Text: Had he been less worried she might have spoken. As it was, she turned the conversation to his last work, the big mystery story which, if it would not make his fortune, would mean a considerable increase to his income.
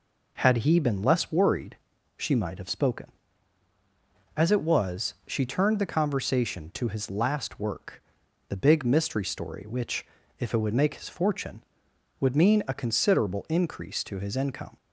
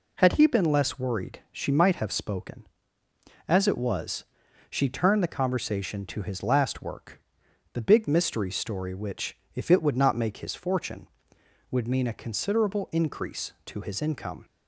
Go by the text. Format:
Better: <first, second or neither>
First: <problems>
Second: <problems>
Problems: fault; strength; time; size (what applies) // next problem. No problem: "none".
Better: second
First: pauses between "worried" and "she"; at 1.7 s; 0.42 s long // skips "not"; at 10.7 s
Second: none